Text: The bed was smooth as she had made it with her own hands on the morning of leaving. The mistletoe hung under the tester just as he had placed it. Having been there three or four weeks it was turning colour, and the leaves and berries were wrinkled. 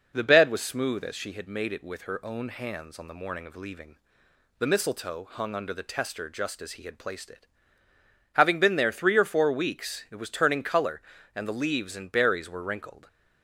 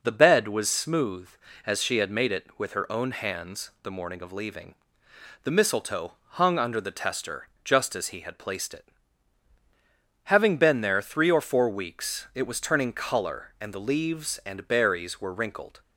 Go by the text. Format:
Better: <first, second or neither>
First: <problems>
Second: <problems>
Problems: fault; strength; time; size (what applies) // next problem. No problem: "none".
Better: first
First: none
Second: skips "on"; at 3.7 s // pauses between "mistletoe" and "hung"; slight; at 6.1 s; 0.17 s long // pauses between "tester" and "just"; slight; at 7.4 s; 0.16 s long